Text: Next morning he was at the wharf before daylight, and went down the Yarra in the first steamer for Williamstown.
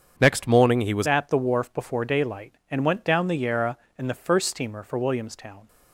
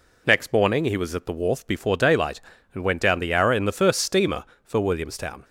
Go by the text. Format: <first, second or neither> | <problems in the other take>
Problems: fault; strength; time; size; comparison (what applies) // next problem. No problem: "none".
second | starts louder than the rest; strong; until 1.1 s; 7.5 dB // changes voice at "at"; from 1.0 s on; 4.6 s long